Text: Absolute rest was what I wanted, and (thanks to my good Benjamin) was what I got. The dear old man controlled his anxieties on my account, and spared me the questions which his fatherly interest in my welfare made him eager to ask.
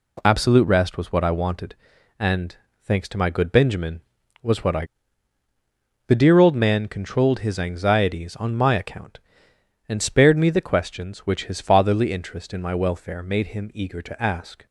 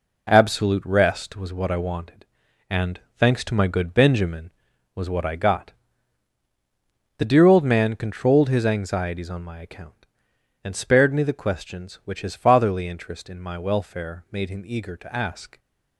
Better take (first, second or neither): second